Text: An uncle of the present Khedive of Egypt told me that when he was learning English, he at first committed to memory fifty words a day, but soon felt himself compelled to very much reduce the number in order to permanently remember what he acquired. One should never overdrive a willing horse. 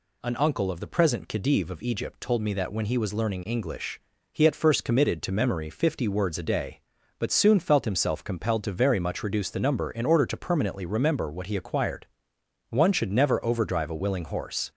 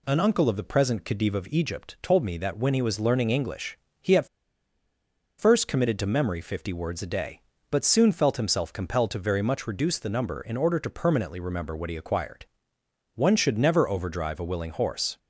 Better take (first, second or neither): first